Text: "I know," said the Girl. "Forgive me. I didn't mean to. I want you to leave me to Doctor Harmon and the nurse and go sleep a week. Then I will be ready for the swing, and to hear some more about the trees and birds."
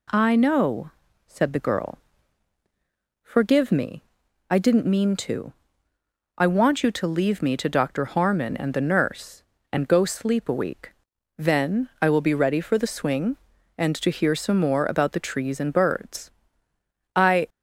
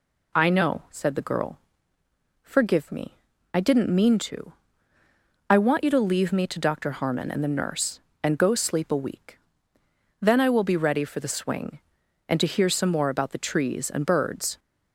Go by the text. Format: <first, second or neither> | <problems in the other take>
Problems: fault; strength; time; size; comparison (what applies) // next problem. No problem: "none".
second | goes on to say "I"; slight; from 17.1 s on; 0.34 s long